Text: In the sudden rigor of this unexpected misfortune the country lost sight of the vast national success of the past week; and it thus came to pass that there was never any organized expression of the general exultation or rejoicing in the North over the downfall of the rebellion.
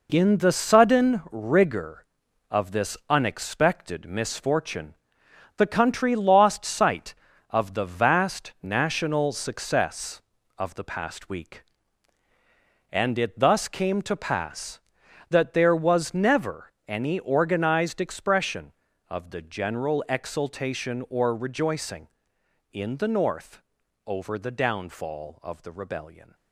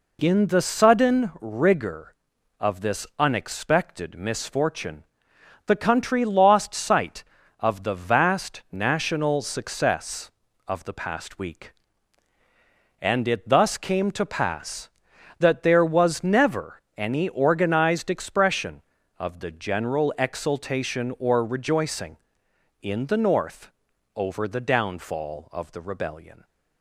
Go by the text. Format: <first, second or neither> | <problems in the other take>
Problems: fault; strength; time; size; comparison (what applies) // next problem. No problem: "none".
second | gets quieter; strong; throughout; 7.5 dB // pauses between "misfortune" and "the"; noticeable; at 4.9 s; 0.60 s long; noticeable in the second // pauses between "never" and "any"; slight; at 16.7 s; 0.16 s long; slight in the second // pauses between "North" and "over"; at 23.6 s; 0.44 s long; also in the second